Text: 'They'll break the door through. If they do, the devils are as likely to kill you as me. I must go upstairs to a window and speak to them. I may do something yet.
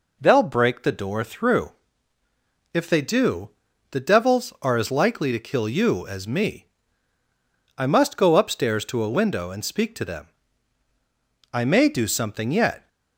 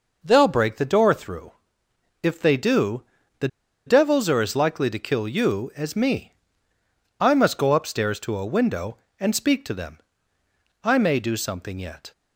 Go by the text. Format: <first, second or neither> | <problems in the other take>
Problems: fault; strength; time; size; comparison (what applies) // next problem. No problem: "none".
first | pauses between "the" and "devils"; at 3.4 s; 0.38 s long